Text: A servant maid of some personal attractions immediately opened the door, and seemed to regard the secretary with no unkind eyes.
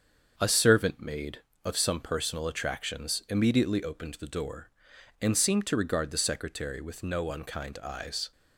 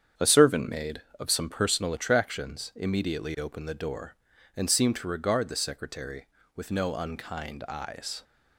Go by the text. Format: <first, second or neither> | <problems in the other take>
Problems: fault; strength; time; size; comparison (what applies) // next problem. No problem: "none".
neither | starts louder than the rest; the same in both